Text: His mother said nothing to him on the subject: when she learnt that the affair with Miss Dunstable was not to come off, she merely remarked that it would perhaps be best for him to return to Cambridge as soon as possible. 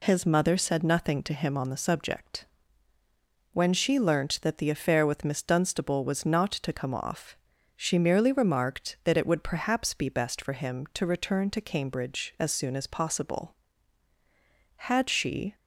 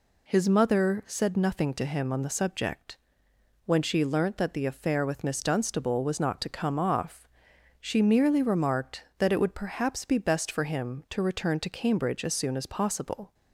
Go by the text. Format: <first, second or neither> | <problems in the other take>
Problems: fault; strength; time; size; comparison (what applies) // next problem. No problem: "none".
second | goes on to say "Had she"; noticeable; from 14.7 s on; 0.80 s long